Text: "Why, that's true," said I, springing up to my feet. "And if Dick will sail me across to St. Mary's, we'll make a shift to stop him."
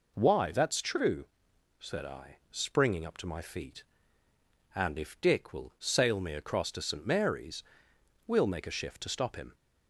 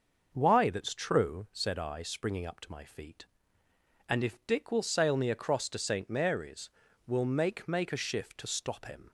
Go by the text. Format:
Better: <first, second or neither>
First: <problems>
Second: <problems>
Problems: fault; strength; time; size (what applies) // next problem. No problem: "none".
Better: first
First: none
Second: starts louder than the rest; noticeable; until 1.3 s; 6 dB // says "make" twice; at 7.6 s